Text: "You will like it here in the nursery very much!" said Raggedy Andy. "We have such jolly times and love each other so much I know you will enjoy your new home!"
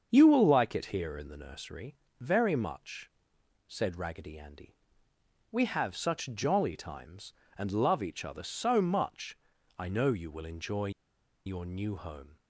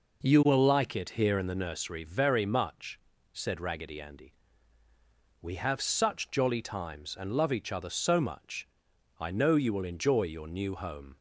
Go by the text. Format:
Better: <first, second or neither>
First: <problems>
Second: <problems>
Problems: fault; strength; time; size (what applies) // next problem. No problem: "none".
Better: second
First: starts louder than the rest; until 1.1 s; 7 dB // pauses between "nursery" and "very"; slight; at 1.9 s; 0.24 s long // pauses between "much" and "I"; at 9.3 s; 0.44 s long // pauses between "enjoy" and "your"; noticeable; at 10.8 s; 0.56 s long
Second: pauses between "much" and "I"; noticeable; at 8.6 s; 0.54 s long